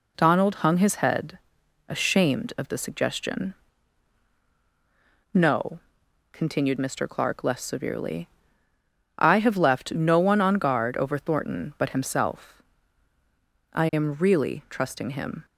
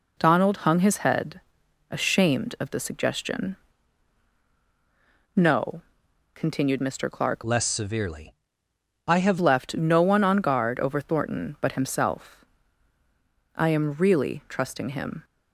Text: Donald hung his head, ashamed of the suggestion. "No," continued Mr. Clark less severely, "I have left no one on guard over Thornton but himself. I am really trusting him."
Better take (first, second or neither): first